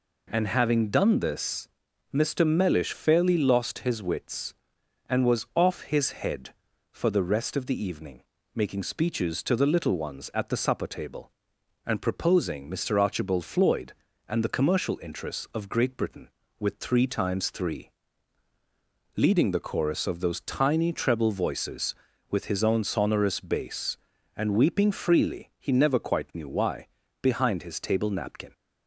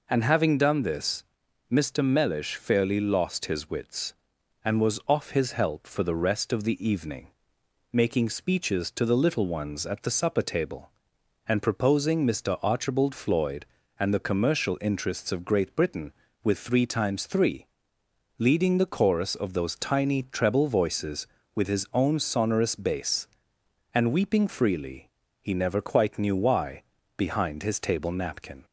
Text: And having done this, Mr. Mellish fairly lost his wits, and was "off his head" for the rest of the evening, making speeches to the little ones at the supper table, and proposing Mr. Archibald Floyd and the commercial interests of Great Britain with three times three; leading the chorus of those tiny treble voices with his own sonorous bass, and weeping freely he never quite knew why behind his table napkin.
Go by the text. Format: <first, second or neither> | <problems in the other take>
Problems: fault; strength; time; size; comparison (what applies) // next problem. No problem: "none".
first | says "help" for "head"; at 5.5 s // pauses between "freely" and "he"; slight; at 25.0 s; 0.32 s long // pauses between "why" and "behind"; slight; at 26.8 s; 0.32 s long; slight in the first